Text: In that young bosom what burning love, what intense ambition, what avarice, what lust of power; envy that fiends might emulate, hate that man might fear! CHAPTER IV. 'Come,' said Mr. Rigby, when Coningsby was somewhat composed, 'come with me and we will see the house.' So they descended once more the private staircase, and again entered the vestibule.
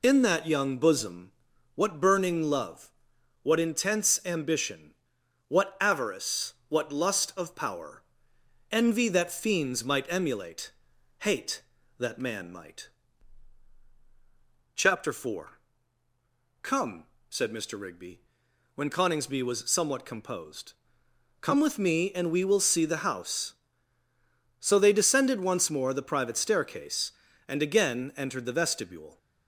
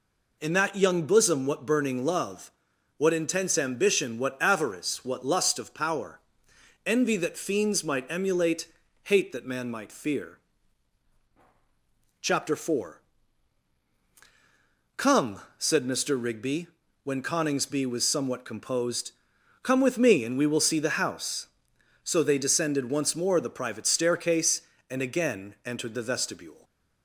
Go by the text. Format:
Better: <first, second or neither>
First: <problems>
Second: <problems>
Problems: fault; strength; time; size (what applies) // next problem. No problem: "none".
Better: second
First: pauses between "bosom" and "what"; at 1.3 s; 0.42 s long // skips "fear"; at 13.8 s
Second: none